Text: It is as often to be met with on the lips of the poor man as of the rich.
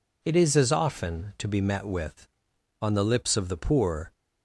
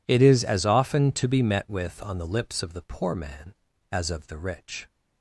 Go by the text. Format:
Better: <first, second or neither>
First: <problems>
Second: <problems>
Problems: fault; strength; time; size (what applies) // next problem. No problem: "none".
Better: second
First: stops before "man as of the rich"; at 4.1 s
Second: none